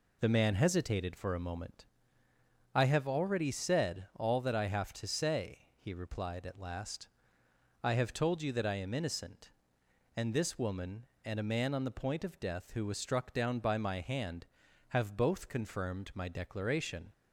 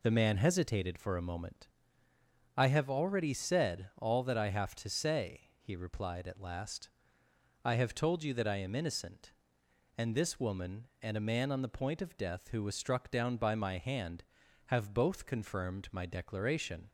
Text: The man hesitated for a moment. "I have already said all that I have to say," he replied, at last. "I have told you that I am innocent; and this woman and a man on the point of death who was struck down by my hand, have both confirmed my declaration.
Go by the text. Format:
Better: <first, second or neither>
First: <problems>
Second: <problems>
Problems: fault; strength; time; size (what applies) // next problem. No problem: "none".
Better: neither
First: none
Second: none